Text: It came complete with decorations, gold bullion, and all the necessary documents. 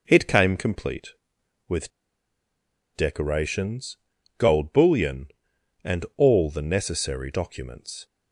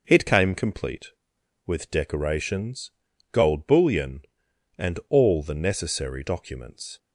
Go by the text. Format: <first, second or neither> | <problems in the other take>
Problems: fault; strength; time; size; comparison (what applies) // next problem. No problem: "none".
second | pauses between "with" and "decorations"; at 1.9 s; 1.0 s long